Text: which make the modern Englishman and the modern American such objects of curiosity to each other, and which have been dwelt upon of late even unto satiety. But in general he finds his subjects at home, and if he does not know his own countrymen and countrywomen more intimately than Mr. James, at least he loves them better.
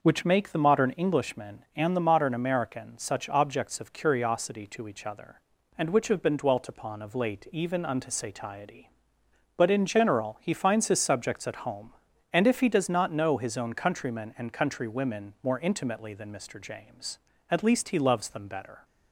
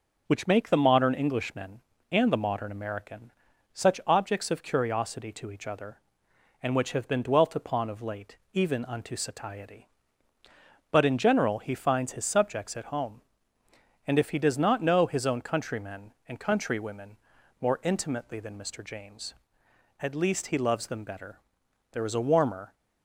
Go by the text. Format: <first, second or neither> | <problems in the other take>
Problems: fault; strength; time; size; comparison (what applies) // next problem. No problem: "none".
first | pauses between "American" and "such"; at 3.3 s; 0.42 s long // pauses between "late" and "even"; slight; at 8.3 s; 0.16 s long // pauses between "countrywomen" and "more"; at 17.1 s; 0.44 s long // goes on to say "There is a warmer"; noticeable; from 21.9 s on; 0.82 s long